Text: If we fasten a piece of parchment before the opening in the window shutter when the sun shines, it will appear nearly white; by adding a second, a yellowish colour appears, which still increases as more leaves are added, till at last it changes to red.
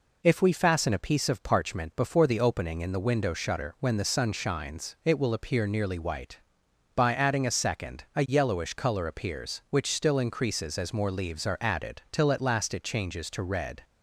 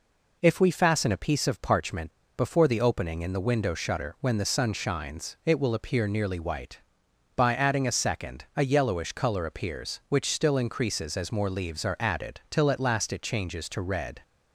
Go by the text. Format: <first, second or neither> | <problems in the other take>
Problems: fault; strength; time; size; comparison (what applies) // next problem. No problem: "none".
first | pauses between "parchment" and "before"; slight; at 2.1 s; 0.23 s long